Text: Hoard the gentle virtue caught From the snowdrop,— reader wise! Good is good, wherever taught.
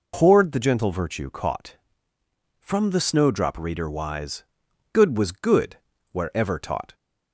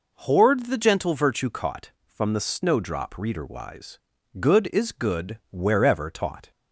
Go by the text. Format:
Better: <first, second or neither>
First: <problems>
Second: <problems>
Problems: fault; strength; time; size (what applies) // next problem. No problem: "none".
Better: second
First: says "was" for "is"; at 5.1 s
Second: none